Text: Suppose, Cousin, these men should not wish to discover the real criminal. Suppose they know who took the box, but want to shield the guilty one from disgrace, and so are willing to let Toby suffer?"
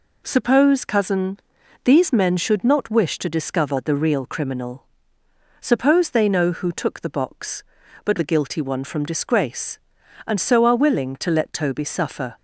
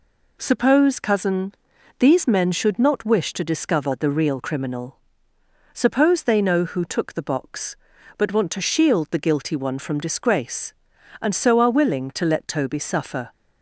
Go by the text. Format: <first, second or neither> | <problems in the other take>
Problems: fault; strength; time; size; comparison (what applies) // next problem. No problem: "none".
second | skips "want to shield"; at 8.1 s